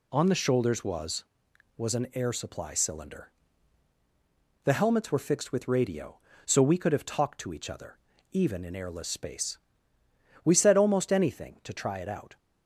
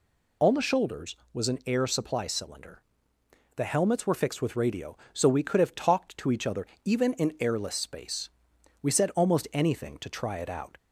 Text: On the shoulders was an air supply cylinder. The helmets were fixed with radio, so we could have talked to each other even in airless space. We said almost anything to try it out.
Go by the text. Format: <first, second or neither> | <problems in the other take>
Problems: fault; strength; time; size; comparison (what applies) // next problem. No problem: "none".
second | says "was" twice; at 1.7 s // pauses between "other" and "even"; slight; at 7.9 s; 0.32 s long; slight in the second